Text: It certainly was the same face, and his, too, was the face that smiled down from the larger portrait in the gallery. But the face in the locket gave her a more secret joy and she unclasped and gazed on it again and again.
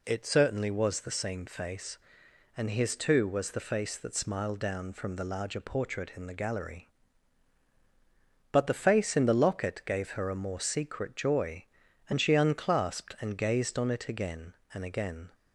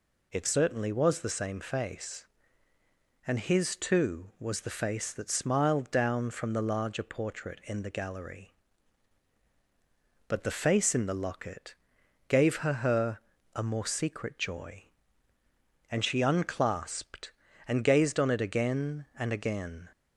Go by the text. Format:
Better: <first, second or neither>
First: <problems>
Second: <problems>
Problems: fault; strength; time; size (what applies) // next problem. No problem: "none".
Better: first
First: none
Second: pauses between "locket" and "gave"; noticeable; at 11.7 s; 0.52 s long // says "her" twice; at 12.7 s